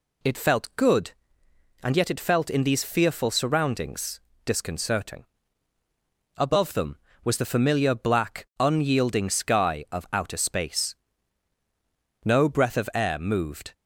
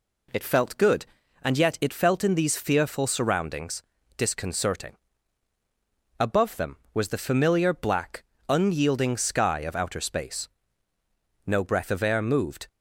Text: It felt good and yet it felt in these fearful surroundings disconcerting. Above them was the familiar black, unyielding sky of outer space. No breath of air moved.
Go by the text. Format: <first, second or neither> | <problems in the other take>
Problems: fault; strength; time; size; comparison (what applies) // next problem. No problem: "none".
neither | pauses between "surroundings" and "disconcerting"; slight; the same in both